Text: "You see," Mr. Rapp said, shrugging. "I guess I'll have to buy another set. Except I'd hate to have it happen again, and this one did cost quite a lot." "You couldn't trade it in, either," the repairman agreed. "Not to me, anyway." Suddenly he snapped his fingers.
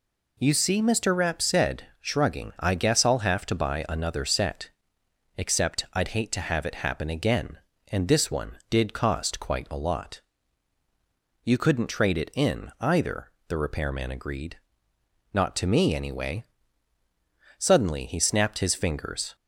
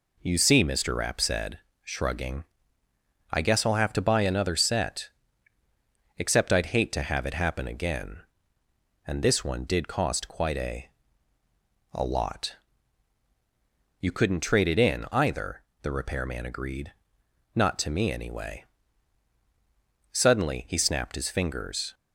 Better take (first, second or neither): first